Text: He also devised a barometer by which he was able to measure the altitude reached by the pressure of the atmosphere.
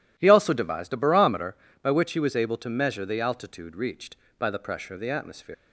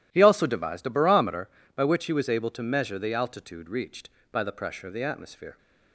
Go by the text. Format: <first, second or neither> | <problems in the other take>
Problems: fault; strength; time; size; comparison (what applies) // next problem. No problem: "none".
second | leaves "atmosphere" unfinished; at 5.5 s; 95 ms